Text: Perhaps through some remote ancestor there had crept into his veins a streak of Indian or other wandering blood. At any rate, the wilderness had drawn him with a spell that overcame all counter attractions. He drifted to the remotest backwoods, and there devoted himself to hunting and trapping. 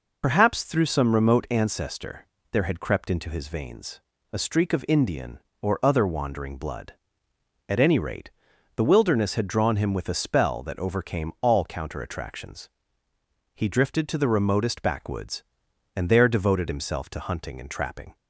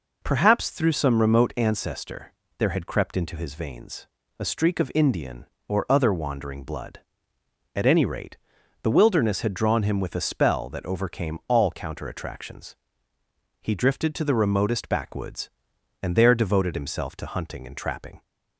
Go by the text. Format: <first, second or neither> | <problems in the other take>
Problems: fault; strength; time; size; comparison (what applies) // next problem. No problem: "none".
second | loses the start of "Perhaps"; at 0.2 s; 75 ms // pauses between "ancestor" and "there"; slight; at 2.2 s; 0.28 s long; slight in the second // pauses between "veins" and "a"; slight; at 4.0 s; 0.32 s long; slight in the second